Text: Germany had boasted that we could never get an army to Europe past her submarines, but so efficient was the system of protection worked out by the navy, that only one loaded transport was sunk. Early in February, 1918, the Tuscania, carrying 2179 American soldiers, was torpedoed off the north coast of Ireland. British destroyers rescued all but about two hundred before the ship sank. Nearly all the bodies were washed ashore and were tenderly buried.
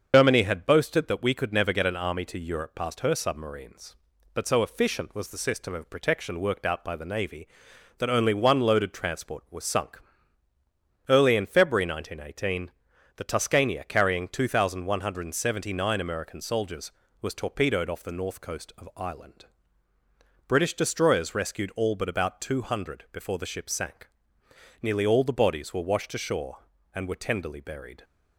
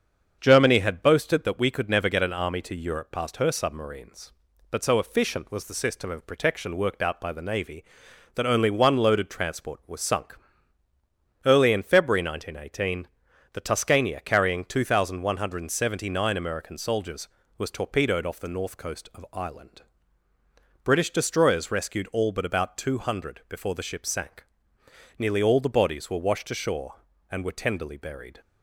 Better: second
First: loses the start of "Germany"; at 0.1 s; 100 ms // starts louder than the rest; until 1.1 s; 6.5 dB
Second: starts louder than the rest; until 1.4 s; 7 dB

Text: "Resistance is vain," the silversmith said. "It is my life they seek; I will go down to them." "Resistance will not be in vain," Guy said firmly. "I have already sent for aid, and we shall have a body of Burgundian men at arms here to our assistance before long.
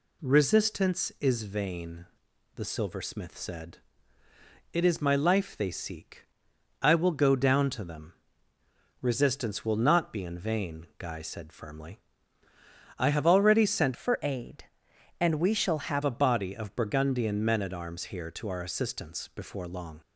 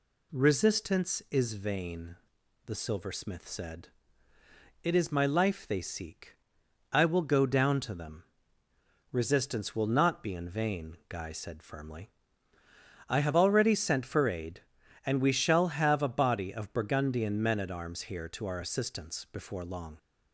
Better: second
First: changes voice from "for" to "have"; from 13.9 to 16.0 s; 2.1 s long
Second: none

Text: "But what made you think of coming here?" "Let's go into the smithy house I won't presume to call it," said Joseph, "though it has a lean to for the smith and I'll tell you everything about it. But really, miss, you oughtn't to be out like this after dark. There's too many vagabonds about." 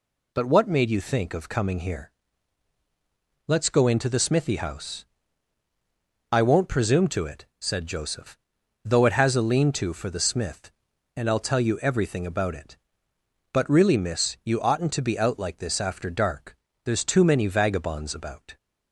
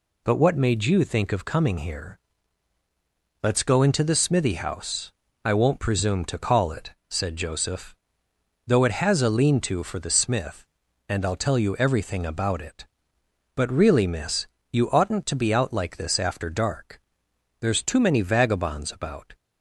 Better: second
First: pauses between "house" and "I"; strong; at 5.0 s; 1.2 s long // skips "call"; at 7.2 s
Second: pauses between "house" and "I"; slight; at 5.1 s; 0.32 s long

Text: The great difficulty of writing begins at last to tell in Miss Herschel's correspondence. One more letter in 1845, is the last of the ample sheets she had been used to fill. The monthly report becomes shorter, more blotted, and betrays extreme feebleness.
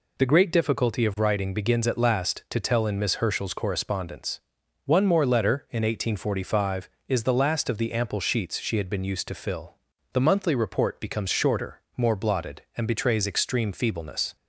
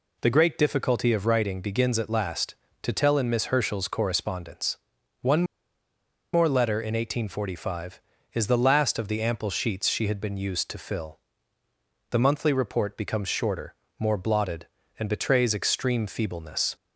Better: first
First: none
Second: pauses between "One" and "more"; noticeable; at 5.4 s; 0.89 s long

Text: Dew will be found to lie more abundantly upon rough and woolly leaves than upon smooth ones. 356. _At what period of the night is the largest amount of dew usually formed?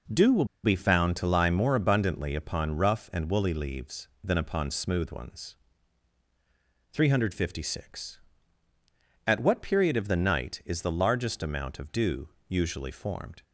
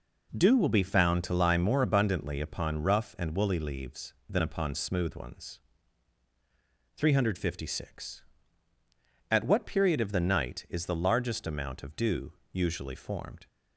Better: second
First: pauses between "will" and "be"; slight; at 0.4 s; 0.19 s long // pauses between "dew" and "usually"; slight; at 12.2 s; 0.18 s long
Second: pauses between "dew" and "usually"; slight; at 12.3 s; 0.18 s long

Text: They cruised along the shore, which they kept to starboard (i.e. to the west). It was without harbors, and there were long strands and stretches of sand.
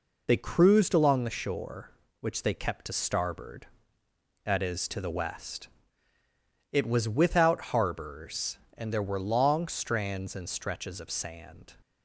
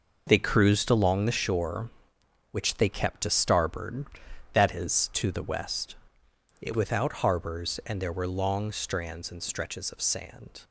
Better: first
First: none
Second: skips "was"; at 6.7 s

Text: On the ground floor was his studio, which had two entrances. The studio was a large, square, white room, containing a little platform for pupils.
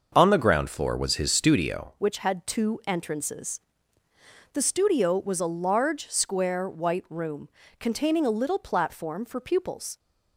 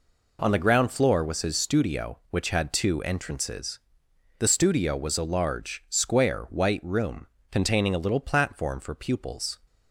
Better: second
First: starts louder than the rest; until 1.1 s; 6 dB // changes voice at "which"; from 1.9 s on; 8.0 s long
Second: none

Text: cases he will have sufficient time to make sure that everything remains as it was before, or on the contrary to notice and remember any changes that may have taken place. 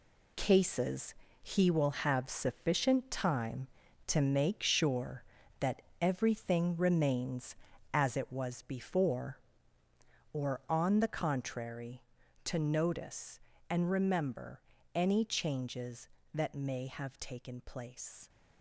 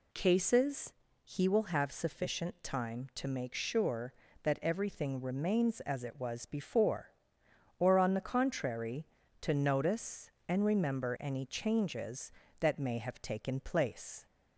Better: second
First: gets quieter; strong; throughout; 8.5 dB // pauses between "cases" and "he"; slight; at 1.1 s; 0.28 s long // pauses between "that" and "everything"; slight; at 5.8 s; 0.18 s long // pauses between "remember" and "any"; slight; at 14.5 s; 0.34 s long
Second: pauses between "cases" and "he"; slight; at 0.9 s; 0.30 s long

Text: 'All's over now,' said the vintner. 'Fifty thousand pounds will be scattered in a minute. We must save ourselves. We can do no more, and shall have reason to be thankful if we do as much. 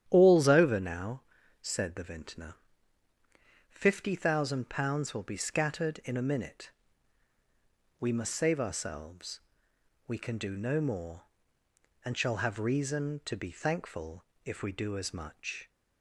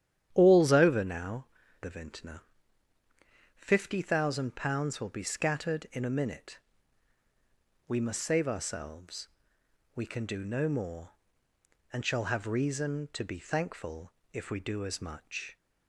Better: first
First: starts louder than the rest; strong; until 1.1 s; 10 dB // pauses between "thankful" and "if"; slight; at 14.2 s; 0.20 s long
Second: starts louder than the rest; strong; until 1.3 s; 10 dB // skips "said"; at 1.6 s // pauses between "thankful" and "if"; slight; at 14.1 s; 0.20 s long

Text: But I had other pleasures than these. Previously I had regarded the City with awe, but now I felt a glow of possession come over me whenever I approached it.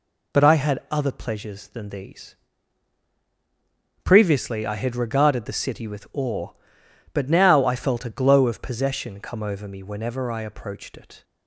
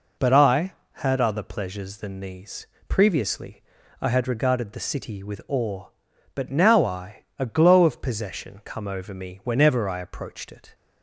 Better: first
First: none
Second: pauses between "Previously" and "I"; at 3.6 s; 0.40 s long // skips "felt"; at 7.3 s

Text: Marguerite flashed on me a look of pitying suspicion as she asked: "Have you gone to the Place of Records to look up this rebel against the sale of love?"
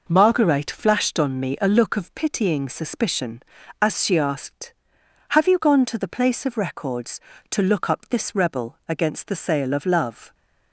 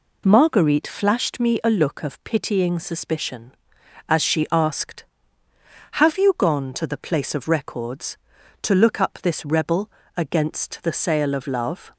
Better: first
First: none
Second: skips "on"; at 1.3 s // pauses between "rebel" and "against"; slight; at 9.9 s; 0.26 s long

